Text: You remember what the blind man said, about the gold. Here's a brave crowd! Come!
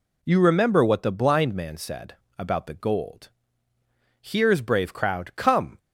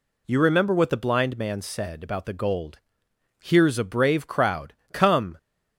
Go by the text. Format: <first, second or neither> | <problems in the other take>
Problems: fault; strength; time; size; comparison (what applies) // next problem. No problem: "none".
second | skips "a"; at 4.6 s